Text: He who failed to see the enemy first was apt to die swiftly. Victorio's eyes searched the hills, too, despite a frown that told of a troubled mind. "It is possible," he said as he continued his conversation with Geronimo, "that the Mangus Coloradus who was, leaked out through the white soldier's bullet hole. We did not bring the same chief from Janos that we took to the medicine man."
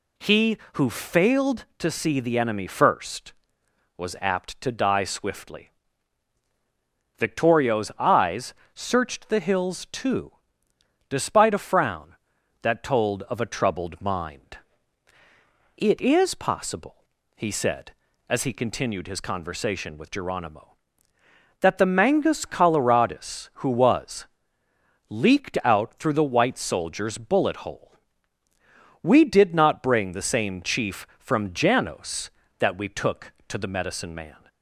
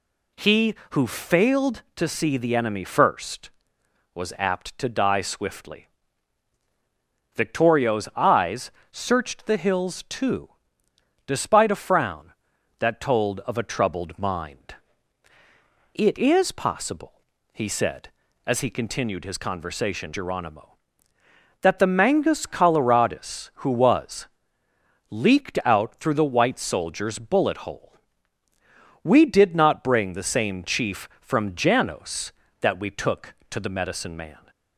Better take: first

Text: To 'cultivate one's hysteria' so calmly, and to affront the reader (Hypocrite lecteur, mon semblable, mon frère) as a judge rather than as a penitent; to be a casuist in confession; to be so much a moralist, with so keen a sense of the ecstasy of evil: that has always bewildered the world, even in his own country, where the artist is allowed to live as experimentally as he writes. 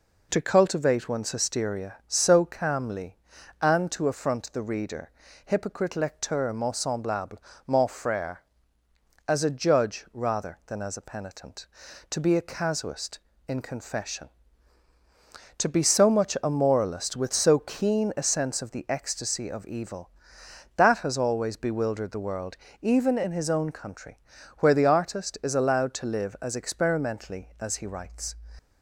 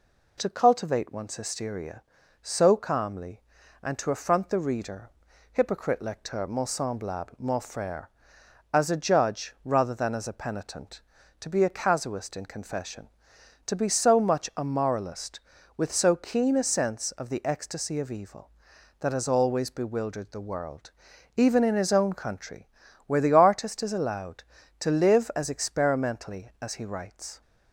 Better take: neither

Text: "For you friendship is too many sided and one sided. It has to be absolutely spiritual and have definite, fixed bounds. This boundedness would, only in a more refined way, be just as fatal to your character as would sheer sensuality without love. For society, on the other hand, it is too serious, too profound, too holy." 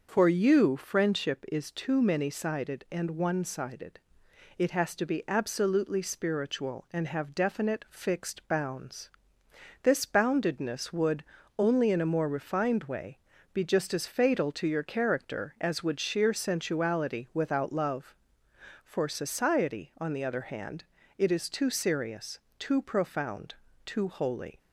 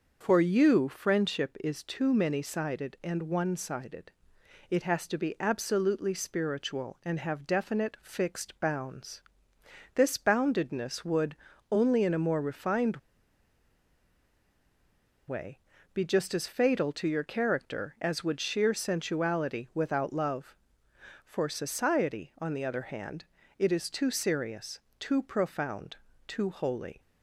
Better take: first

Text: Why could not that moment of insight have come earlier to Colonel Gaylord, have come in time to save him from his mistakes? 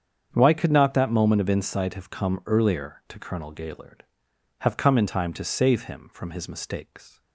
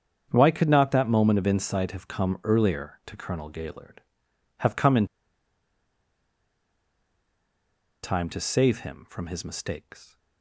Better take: first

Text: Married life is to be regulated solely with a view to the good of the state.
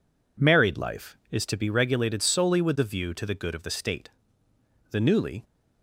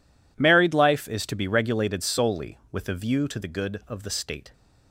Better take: second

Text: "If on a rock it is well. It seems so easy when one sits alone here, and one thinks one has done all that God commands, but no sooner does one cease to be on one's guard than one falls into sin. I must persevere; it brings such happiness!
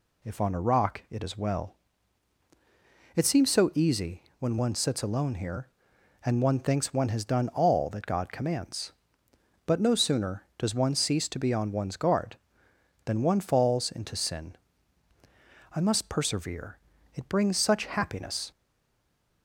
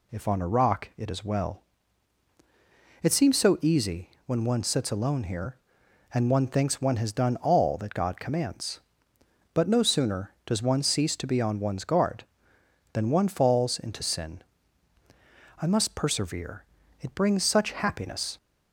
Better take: second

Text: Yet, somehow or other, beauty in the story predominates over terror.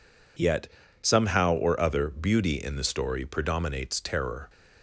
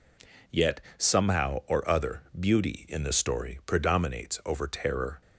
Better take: second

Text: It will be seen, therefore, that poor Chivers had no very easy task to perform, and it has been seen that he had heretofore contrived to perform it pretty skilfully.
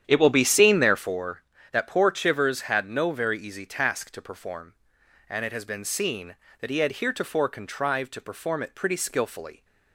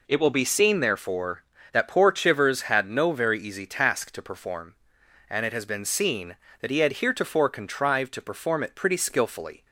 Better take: second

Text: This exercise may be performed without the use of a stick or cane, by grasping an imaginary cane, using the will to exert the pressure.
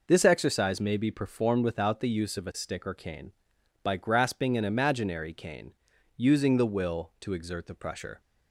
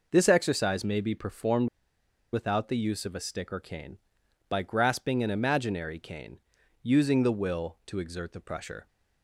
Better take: first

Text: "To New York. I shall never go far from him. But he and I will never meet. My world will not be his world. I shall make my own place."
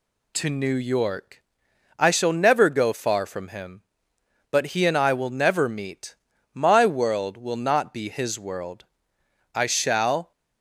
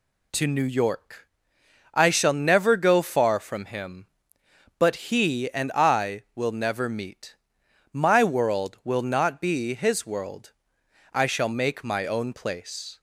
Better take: second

